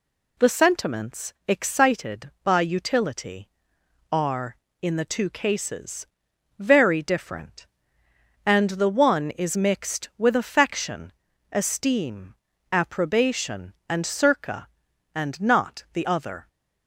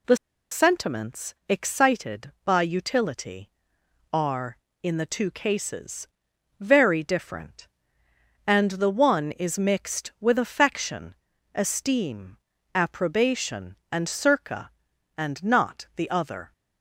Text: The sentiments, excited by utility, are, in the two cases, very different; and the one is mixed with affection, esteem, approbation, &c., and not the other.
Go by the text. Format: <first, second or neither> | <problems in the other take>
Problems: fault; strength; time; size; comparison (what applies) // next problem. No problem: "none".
first | pauses between "The" and "sentiments"; slight; at 0.1 s; 0.34 s long